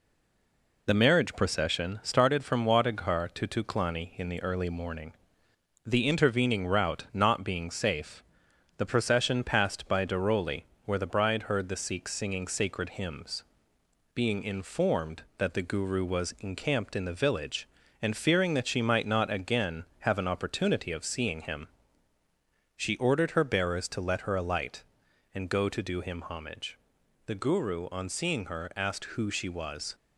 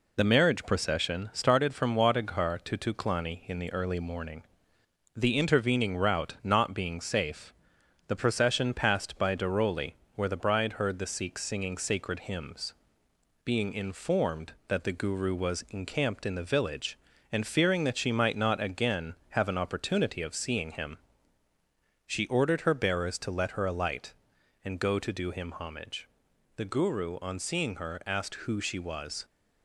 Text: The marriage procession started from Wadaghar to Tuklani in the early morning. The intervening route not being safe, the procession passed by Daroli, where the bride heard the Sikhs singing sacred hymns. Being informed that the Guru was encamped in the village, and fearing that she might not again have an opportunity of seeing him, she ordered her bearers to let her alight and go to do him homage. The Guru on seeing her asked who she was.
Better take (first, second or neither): second